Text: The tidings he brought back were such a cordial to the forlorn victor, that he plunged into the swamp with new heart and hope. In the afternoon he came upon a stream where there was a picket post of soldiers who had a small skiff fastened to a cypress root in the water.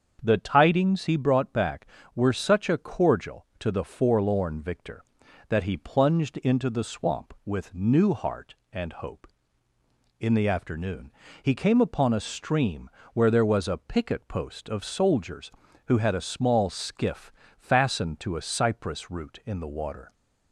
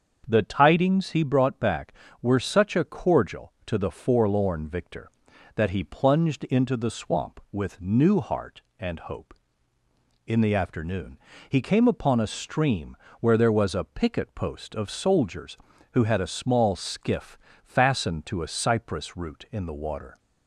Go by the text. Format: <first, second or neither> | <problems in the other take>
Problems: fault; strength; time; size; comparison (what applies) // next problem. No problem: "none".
neither | starts louder than the rest; the same in both // pauses between "afternoon" and "he"; slight; the same in both // pauses between "stream" and "where"; slight; the same in both // pauses between "skiff" and "fastened"; slight; the same in both